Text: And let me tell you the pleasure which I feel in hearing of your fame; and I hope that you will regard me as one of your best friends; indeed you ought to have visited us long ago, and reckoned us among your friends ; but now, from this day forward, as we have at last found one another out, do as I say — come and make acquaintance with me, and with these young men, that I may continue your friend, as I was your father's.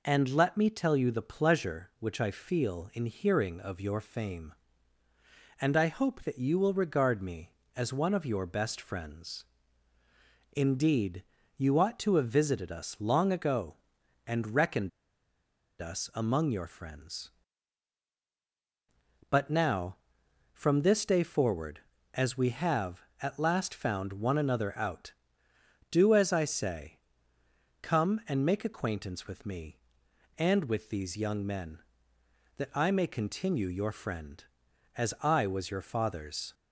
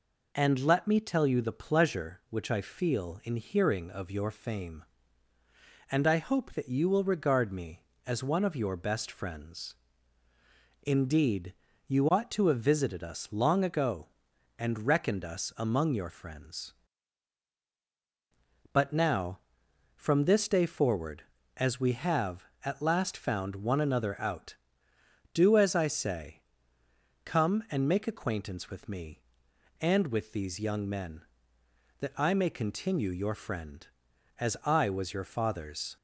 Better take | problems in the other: second | pauses between "indeed" and "you"; slight; at 11.2 s; 0.32 s long; slight in the second // pauses between "reckoned" and "us"; noticeable; at 14.8 s; 0.91 s long

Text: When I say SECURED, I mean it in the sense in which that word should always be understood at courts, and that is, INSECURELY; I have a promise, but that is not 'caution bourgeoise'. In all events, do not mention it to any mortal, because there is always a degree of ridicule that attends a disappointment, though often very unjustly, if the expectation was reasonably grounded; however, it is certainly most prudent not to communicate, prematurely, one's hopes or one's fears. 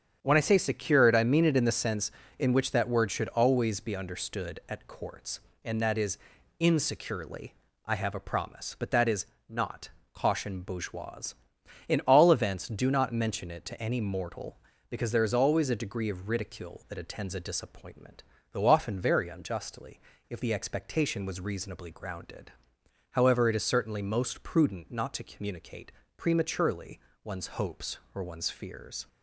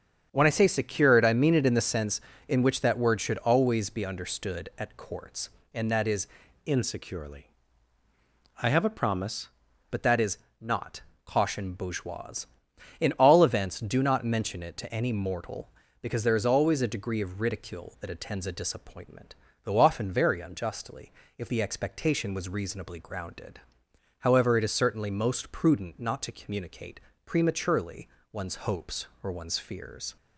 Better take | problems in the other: first | starts louder than the rest; strong; until 1.3 s; 8 dB; strong in the first // changes voice from "INSECURELY" to "promise"; from 6.6 to 9.5 s; 2.9 s long // pauses between "is" and "not"; slight; at 10.3 s; 0.22 s long; slight in the first // pauses between "not" and "caution"; slight; at 11.0 s; 0.24 s long; slight in the first

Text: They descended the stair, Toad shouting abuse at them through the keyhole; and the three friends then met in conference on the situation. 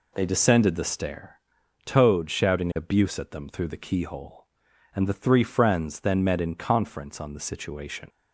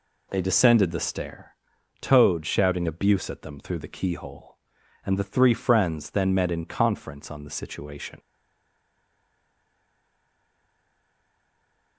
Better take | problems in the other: first | stays silent after the last word; strong; from 8.1 s on; 3.8 s long

